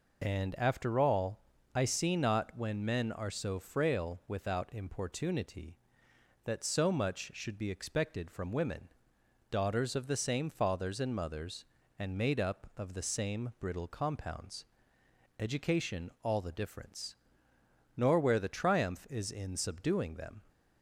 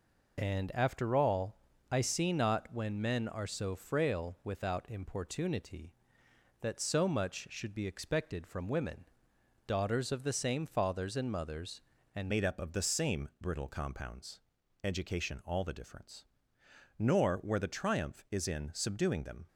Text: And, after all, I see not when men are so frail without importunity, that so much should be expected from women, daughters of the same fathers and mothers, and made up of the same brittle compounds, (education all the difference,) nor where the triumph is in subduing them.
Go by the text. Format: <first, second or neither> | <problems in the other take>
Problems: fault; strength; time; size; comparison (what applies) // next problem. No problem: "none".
first | changes voice at "made"; from 12.2 s on; 7.2 s long